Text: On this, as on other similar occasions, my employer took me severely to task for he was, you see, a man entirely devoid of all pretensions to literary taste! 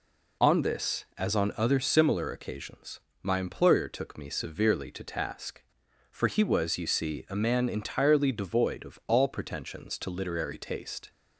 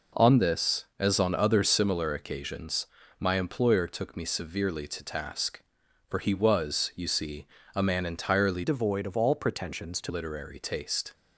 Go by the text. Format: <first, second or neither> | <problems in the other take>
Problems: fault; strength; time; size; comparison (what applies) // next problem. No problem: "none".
first | changes voice from "devoid" to "to"; from 8.6 to 10.1 s; 1.5 s long